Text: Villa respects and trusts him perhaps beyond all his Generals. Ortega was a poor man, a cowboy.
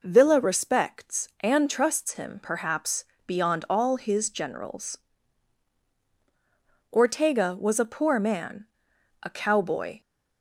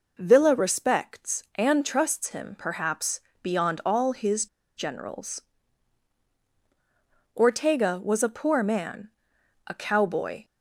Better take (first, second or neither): first